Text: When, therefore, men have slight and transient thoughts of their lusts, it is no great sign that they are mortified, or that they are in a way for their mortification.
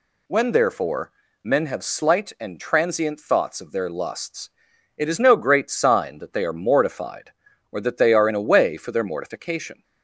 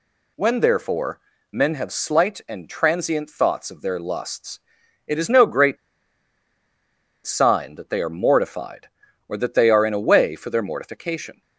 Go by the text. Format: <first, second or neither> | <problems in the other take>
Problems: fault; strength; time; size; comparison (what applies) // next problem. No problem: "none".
first | pauses between "great" and "sign"; strong; at 5.7 s; 1.4 s long